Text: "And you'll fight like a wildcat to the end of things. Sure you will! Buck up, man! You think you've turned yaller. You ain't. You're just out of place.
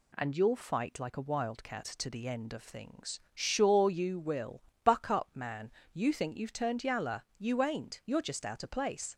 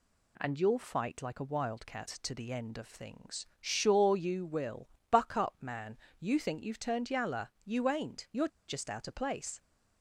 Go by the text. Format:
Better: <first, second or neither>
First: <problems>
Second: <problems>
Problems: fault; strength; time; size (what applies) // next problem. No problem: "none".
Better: first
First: none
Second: pauses between "You're" and "just"; slight; at 8.4 s; 0.19 s long